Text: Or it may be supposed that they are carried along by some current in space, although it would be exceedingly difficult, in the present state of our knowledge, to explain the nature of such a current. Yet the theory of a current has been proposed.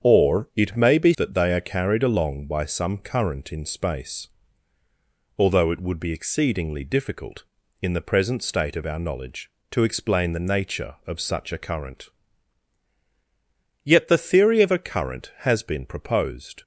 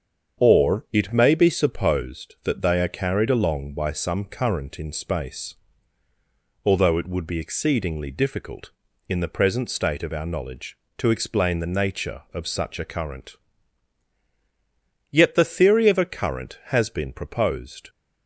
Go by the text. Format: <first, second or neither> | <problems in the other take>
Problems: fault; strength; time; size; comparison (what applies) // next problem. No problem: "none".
second | starts louder than the rest; strong; until 1.1 s; 7.5 dB; strong in the second // skips "supposed"; at 1.1 s